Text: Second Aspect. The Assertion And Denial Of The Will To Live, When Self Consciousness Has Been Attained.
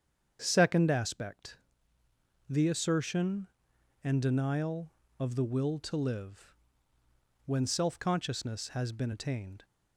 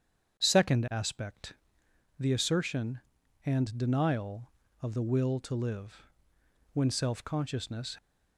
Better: first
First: starts louder than the rest; strong; until 1.4 s; 7.5 dB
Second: starts louder than the rest; strong; until 1.4 s; 8 dB // stops before "Has Been Attained"; at 7.9 s

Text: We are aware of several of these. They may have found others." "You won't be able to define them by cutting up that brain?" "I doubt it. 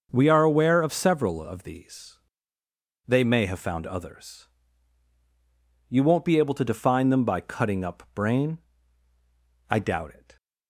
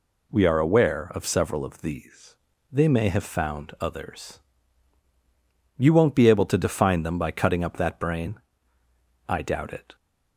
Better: second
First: starts louder than the rest; until 1.1 s; 6 dB // skips "that"; at 8.0 s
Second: none

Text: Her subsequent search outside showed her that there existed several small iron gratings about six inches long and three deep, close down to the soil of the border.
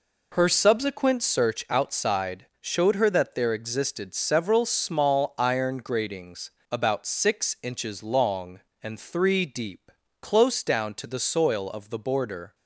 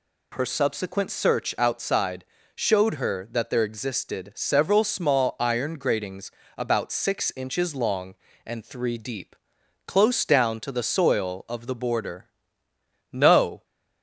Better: first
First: pauses between "gratings" and "about"; slight; at 6.4 s; 0.22 s long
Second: pauses between "outside" and "showed"; slight; at 2.2 s; 0.30 s long // pauses between "gratings" and "about"; slight; at 6.3 s; 0.26 s long // goes on to say "No"; from 13.1 s on; 0.52 s long

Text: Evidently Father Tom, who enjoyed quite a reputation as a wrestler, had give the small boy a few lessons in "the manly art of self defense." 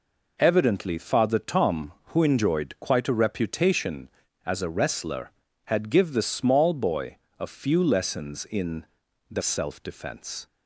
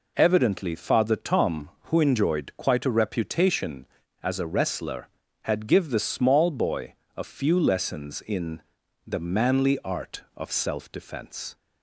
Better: second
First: pauses between "boy" and "a"; slight; at 7.1 s; 0.24 s long // pauses between "in" and "the"; noticeable; at 8.8 s; 0.46 s long // skips "manly art of"; at 9.4 s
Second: pauses between "boy" and "a"; slight; at 6.9 s; 0.24 s long // pauses between "in" and "the"; noticeable; at 8.6 s; 0.46 s long

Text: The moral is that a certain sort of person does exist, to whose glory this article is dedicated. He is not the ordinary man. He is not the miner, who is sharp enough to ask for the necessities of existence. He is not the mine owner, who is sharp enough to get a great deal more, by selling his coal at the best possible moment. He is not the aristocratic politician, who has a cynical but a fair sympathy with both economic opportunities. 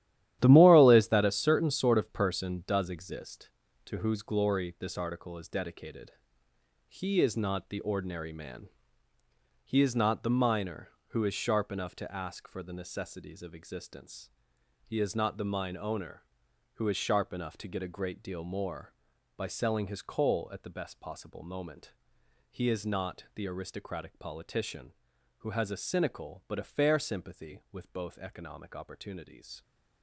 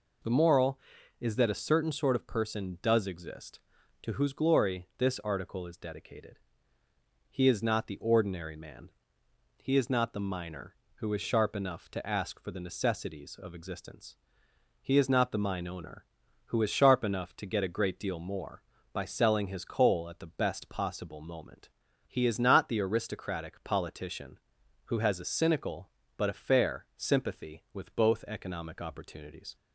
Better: second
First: gets quieter; strong; throughout; 10.5 dB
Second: none

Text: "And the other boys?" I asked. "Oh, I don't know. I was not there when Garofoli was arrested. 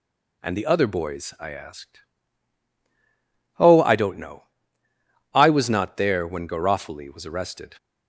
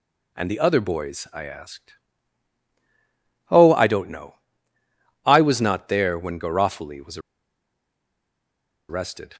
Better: first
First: none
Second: pauses between "was" and "arrested"; strong; at 7.1 s; 1.7 s long

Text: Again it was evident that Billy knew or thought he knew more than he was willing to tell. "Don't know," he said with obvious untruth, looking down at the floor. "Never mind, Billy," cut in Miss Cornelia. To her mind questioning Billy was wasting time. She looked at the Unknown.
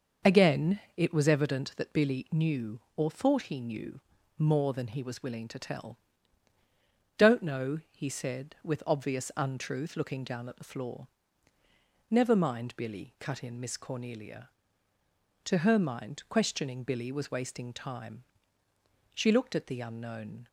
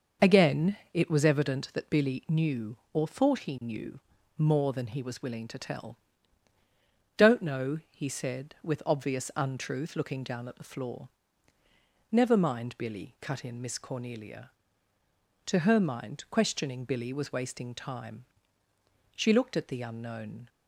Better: neither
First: starts louder than the rest; noticeable; until 1.4 s; 6 dB // pauses between "Again" and "it"; slight; at 0.7 s; 0.16 s long // pauses between "knew" and "more"; at 3.9 s; 0.40 s long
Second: starts louder than the rest; noticeable; until 1.3 s; 6 dB // pauses between "Again" and "it"; slight; at 0.7 s; 0.16 s long // pauses between "knew" and "more"; at 3.9 s; 0.40 s long

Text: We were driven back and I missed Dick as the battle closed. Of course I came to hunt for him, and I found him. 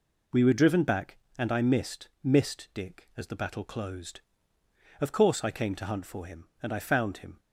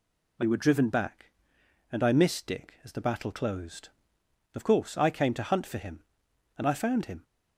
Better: second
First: says "missed" twice; at 2.2 s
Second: none

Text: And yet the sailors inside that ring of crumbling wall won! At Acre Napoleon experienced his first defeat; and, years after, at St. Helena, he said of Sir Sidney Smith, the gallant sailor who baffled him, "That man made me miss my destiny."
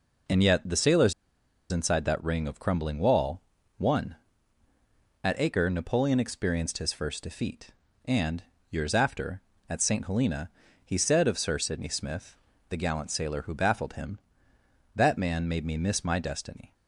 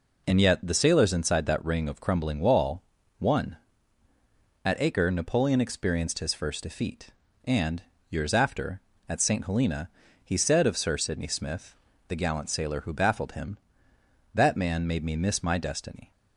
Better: second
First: pauses between "sailors" and "inside"; noticeable; at 1.1 s; 0.57 s long // pauses between "wall" and "won"; at 3.4 s; 0.38 s long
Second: pauses between "wall" and "won"; at 2.8 s; 0.38 s long

